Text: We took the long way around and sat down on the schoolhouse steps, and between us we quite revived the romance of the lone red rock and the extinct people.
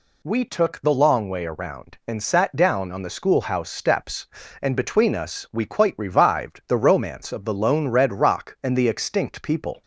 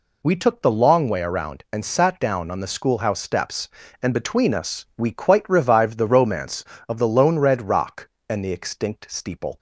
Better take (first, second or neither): first